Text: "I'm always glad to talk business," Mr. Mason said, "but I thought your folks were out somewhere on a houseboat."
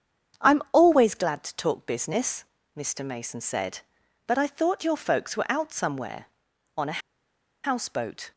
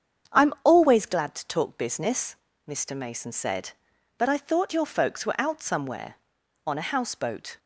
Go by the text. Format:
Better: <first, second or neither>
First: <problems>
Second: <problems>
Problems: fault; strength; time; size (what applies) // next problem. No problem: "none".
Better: second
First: starts louder than the rest; strong; until 1.5 s; 7.5 dB // pauses between "a" and "houseboat"; noticeable; at 6.9 s; 0.64 s long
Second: starts louder than the rest; strong; until 1.4 s; 7.5 dB